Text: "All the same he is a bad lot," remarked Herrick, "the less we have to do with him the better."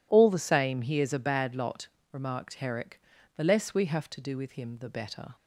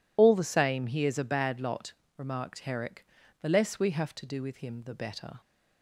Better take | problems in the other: first | loses the start of "All"; at 0.1 s; 35 ms

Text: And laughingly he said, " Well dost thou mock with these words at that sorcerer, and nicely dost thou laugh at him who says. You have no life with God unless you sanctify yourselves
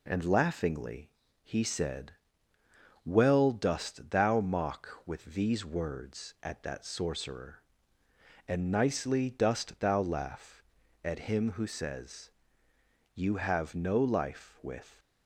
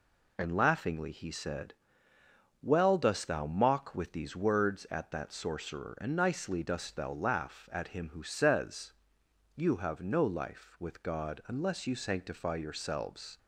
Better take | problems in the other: second | pauses between "laughingly" and "he"; slight; at 1.1 s; 0.32 s long // stops before "God unless you sanctify yourselves"; at 14.9 s

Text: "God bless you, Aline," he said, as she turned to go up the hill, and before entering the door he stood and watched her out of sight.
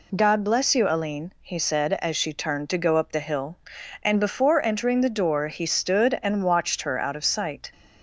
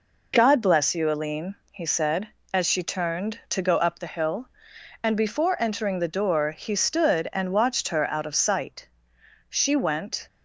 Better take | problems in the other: first | goes on to say "She went"; noticeable; from 9.4 s on; 0.78 s long

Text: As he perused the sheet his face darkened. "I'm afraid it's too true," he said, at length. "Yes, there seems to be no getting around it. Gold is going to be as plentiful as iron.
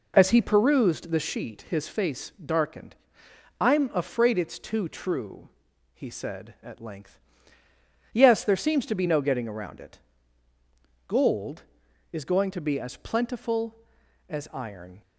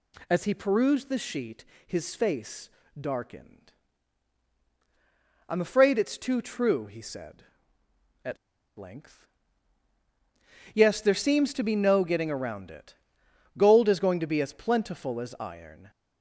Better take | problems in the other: first | pauses between "sheet" and "his"; slight; at 1.6 s; 0.22 s long // pauses between "face" and "darkened"; slight; at 2.6 s; 0.30 s long // pauses between "at" and "length"; at 8.3 s; 0.40 s long

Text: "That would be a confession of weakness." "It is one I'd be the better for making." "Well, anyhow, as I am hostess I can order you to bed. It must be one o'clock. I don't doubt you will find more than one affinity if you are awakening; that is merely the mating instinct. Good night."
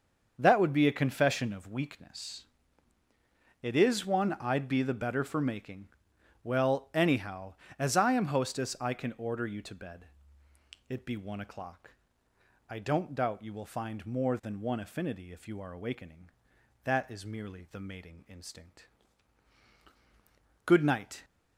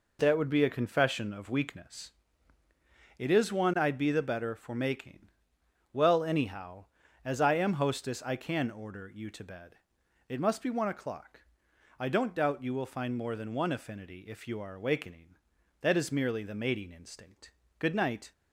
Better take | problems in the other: second | starts louder than the rest; until 1.3 s; 6.5 dB // skips "must"; at 11.0 s

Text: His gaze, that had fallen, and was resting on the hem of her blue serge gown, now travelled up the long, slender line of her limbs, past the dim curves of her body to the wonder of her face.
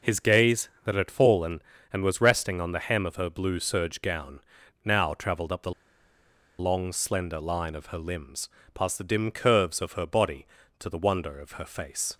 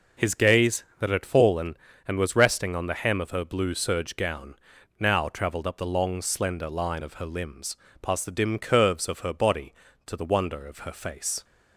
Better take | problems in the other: second | pauses between "the" and "long"; noticeable; at 5.7 s; 0.87 s long

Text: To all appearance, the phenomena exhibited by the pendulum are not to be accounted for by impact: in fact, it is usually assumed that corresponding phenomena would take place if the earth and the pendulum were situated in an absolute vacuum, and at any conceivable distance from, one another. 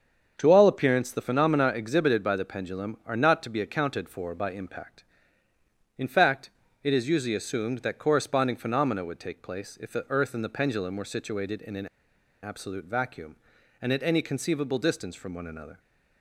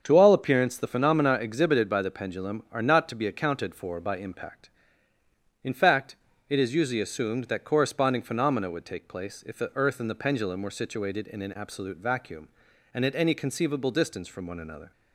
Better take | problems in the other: second | starts louder than the rest; until 1.3 s; 7 dB; also in the second // pauses between "an" and "absolute"; noticeable; at 11.8 s; 0.56 s long

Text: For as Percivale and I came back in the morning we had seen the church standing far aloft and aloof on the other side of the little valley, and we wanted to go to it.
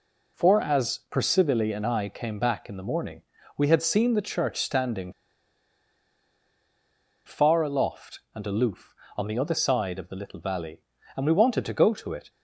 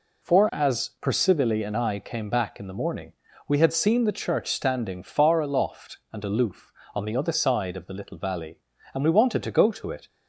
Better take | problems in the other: second | pauses between "morning" and "we"; slight; at 3.2 s; 0.36 s long; slight in the second // pauses between "standing" and "far"; strong; at 5.1 s; 2.1 s long

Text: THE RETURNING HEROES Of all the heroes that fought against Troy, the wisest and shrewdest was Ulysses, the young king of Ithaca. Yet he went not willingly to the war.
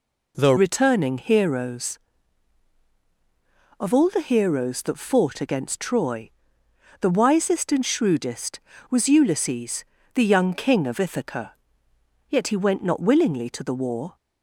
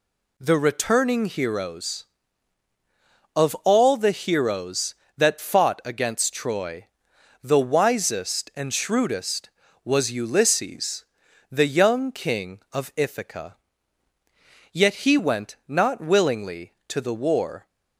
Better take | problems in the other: second | changes voice at "RETURNING"; from 0.5 s on; 13.6 s long

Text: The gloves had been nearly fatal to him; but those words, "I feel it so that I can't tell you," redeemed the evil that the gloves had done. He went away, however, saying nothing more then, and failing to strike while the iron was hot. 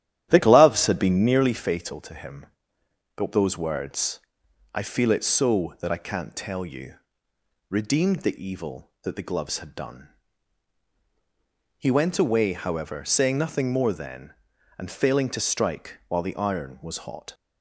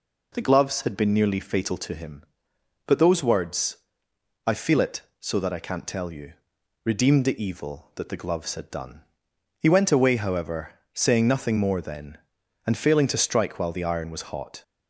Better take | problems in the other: second | starts louder than the rest; strong; until 1.6 s; 11.5 dB

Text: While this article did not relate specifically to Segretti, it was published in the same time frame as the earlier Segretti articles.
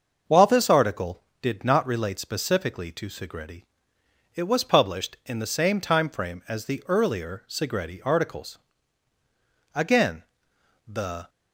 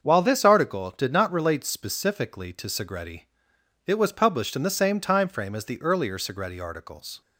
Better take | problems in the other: second | starts louder than the rest; until 1.4 s; 6.5 dB; also in the second // goes on to say "Again the"; from 9.7 s on; 1.5 s long

